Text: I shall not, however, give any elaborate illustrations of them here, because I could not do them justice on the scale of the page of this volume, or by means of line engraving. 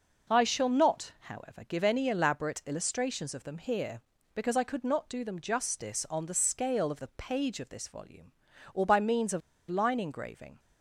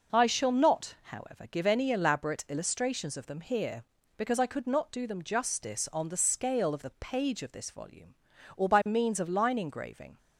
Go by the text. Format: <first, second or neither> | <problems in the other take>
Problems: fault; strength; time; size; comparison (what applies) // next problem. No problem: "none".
second | pauses between "of" and "line"; slight; at 9.4 s; 0.28 s long